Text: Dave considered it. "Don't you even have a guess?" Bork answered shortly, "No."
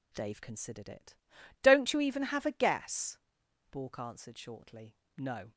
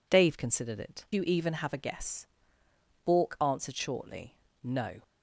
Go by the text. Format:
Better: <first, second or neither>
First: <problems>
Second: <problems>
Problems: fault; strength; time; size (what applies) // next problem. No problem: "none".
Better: first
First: none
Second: skips "Don't"; at 1.0 s